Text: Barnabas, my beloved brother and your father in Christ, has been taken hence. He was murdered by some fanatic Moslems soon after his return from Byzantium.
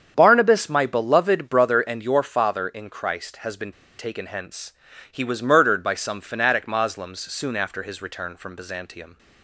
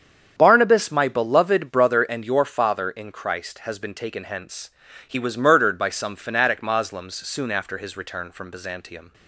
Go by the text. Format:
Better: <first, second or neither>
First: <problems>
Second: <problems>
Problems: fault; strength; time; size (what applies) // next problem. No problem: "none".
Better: second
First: starts louder than the rest; strong; until 1.1 s; 8 dB // pauses between "been" and "taken"; slight; at 3.7 s; 0.24 s long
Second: starts louder than the rest; strong; until 1.3 s; 8 dB